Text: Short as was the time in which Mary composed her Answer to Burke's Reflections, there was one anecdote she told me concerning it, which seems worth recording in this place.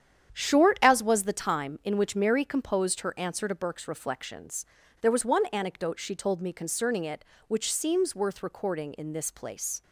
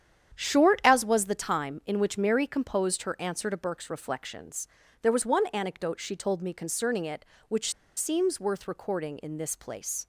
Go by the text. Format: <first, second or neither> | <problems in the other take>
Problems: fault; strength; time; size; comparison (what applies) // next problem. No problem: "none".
first | starts louder than the rest; strong; until 1.3 s; 9 dB; strong in the first // pauses between "which" and "seems"; slight; at 7.7 s; 0.24 s long